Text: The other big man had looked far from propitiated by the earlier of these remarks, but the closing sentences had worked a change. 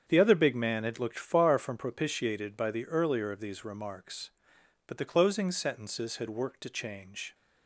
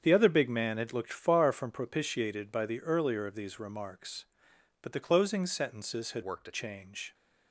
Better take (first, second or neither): first